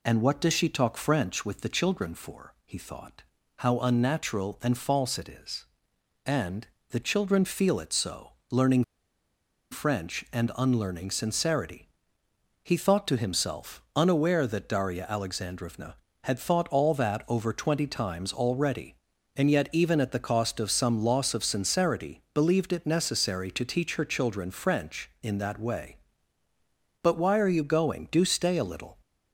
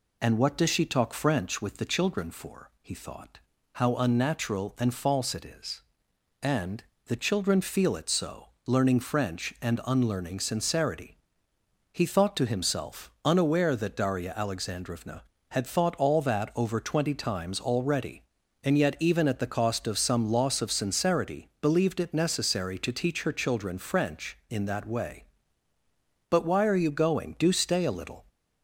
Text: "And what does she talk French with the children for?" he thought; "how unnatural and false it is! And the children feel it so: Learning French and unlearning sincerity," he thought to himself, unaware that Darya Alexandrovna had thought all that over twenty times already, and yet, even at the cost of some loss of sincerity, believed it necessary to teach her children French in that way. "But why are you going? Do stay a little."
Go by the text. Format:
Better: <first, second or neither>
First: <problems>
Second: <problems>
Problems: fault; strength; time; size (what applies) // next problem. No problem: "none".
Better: second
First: pauses between "And" and "the"; slight; at 6.6 s; 0.24 s long // pauses between "Learning" and "French"; noticeable; at 8.8 s; 0.89 s long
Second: pauses between "And" and "the"; slight; at 6.8 s; 0.24 s long